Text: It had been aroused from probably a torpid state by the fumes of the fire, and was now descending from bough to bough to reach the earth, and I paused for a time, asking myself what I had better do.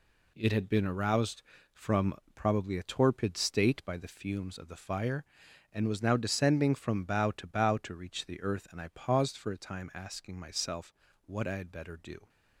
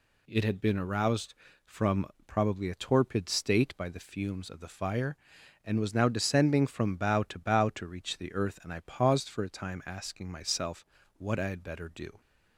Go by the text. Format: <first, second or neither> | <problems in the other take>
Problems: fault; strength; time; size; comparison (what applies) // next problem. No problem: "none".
second | gets quieter; strong; throughout; 8 dB // pauses between "from" and "probably"; slight; at 2.1 s; 0.20 s long; slight in the second // pauses between "myself" and "what"; slight; at 10.9 s; 0.34 s long; slight in the second